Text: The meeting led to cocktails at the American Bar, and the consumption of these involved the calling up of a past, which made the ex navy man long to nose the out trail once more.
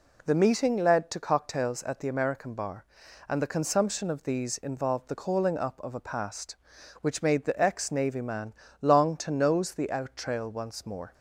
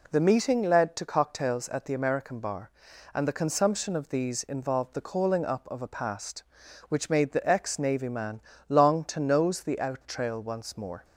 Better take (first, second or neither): neither